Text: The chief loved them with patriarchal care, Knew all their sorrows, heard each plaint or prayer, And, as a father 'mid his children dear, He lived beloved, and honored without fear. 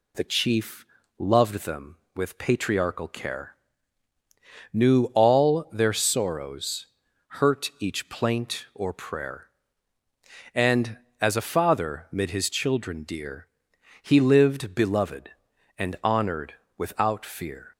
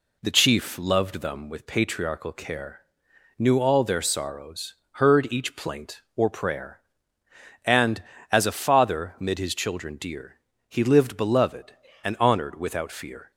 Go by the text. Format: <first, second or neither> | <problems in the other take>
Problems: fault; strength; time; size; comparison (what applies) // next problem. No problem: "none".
second | pauses between "chief" and "loved"; slight; at 0.8 s; 0.32 s long // says "hurt" for "heard"; at 7.2 s // pauses between "honored" and "without"; slight; at 16.5 s; 0.24 s long